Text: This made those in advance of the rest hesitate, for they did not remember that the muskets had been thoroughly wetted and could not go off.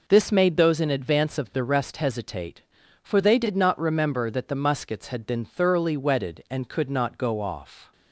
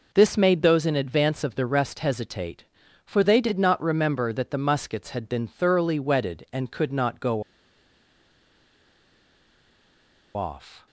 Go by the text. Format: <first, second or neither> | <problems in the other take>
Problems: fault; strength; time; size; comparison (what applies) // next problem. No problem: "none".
first | pauses between "go" and "off"; strong; at 7.4 s; 2.9 s long